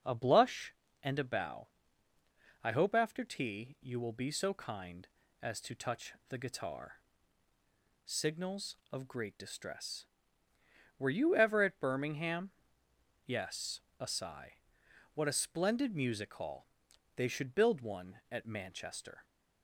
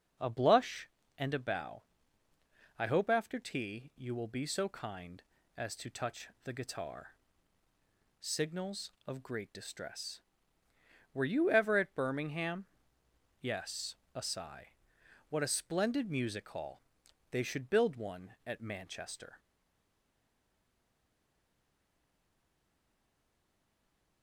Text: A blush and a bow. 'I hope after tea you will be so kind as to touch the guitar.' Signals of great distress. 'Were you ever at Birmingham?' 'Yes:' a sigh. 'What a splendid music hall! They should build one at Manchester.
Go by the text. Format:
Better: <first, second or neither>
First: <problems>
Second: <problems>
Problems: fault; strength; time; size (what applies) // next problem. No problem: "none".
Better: first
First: starts louder than the rest; noticeable; until 1.3 s; 6 dB // pauses between "touch" and "the"; slight; at 6.1 s; 0.16 s long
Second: starts louder than the rest; noticeable; until 1.5 s; 6 dB // pauses between "touch" and "the"; slight; at 6.2 s; 0.16 s long // stays silent after the last word; strong; from 19.3 s on; 4.9 s long